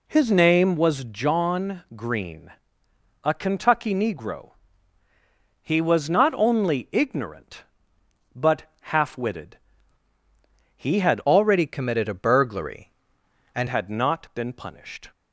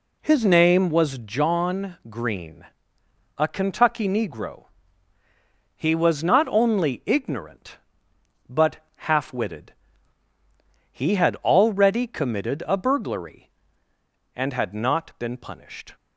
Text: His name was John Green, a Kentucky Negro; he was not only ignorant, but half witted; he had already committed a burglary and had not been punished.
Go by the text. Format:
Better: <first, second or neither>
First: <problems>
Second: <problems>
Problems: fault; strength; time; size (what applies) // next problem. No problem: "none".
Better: second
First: pauses between "but" and "half"; slight; at 8.6 s; 0.16 s long // changes voice from "already" to "and"; from 11.2 to 13.6 s; 2.4 s long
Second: pauses between "but" and "half"; slight; at 8.7 s; 0.17 s long